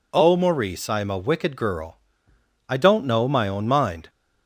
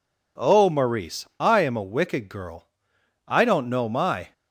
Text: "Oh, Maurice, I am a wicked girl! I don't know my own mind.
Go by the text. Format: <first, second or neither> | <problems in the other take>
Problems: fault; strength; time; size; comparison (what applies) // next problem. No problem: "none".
first | stops before "own mind"; at 4.3 s